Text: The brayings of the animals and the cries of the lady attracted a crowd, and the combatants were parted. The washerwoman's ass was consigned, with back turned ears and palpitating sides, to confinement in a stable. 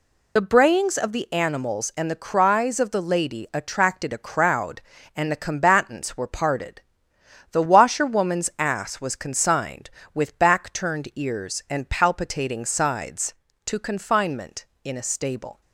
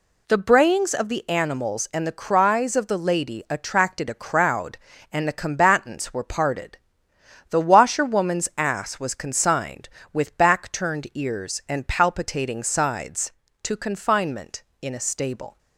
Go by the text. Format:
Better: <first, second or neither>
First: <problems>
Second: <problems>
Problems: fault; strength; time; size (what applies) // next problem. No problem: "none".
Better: second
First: loses the start of "The"; at 0.3 s; 45 ms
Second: none